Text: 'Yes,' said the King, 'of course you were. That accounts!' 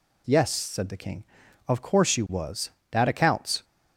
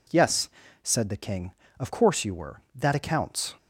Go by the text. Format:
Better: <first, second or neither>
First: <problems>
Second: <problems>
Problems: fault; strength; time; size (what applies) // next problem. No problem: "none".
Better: second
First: says "was" for "were"; at 2.2 s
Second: none